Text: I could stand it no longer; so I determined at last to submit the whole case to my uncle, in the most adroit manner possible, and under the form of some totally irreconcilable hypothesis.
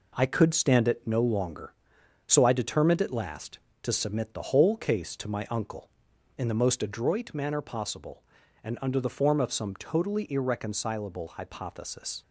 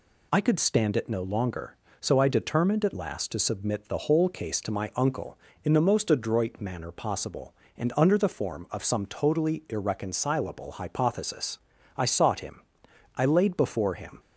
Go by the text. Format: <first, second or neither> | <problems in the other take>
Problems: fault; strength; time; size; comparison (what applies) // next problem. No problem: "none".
first | goes on to say "I sought him I laid before him"; strong; from 11.9 s on; 2.2 s long